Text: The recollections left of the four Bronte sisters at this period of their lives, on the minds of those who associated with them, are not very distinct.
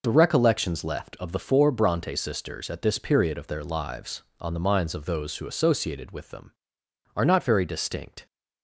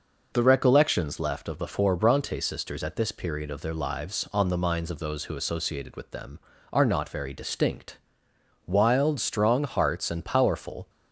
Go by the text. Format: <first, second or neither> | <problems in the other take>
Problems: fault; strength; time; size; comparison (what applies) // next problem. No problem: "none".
first | goes on to say "Wild strong hearts and powerful"; strong; from 8.6 s on; 2.2 s long